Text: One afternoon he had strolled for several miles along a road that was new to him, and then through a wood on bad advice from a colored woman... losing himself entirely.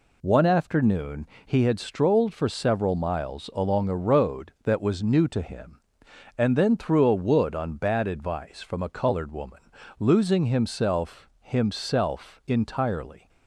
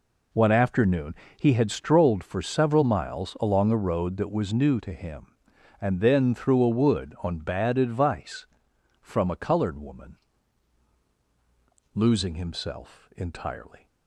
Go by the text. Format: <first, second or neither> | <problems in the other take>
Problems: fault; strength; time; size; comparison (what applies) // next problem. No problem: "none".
second | pauses between "afternoon" and "he"; slight; at 1.2 s; 0.20 s long; slight in the second // says "himself" twice; at 11.4 s